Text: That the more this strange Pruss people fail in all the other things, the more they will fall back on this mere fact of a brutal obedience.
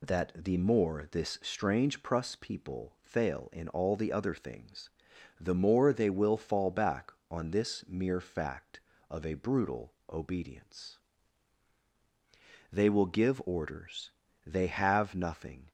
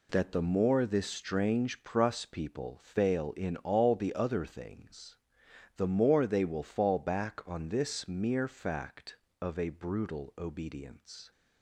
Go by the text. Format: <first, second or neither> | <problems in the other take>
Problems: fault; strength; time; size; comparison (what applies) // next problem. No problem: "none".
second | pauses between "brutal" and "obedience"; slight; at 9.9 s; 0.18 s long // goes on to say "They will give orders they have nothing"; strong; from 12.6 s on; 3.0 s long